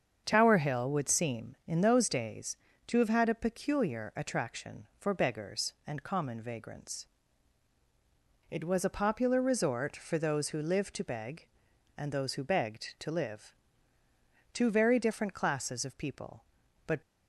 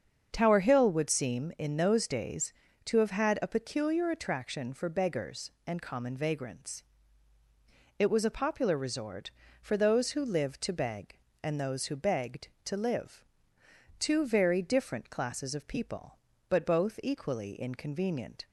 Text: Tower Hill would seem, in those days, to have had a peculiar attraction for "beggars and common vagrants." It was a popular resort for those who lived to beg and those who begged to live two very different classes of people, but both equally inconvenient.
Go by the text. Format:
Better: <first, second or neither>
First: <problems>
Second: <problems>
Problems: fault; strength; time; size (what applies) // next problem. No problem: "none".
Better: second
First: starts louder than the rest; strong; until 1.2 s; 7 dB // pauses between "live" and "two"; at 13.5 s; 1.0 s long // stops before "both equally inconvenient"; at 17.0 s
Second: starts louder than the rest; until 1.3 s; 7 dB // pauses between "live" and "two"; noticeable; at 13.2 s; 0.74 s long